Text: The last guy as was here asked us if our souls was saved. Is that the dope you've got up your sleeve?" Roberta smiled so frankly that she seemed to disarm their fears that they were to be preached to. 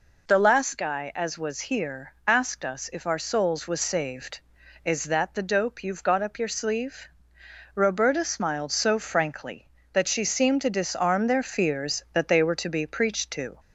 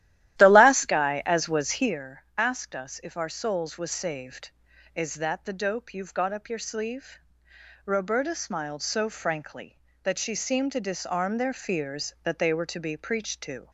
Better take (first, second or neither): first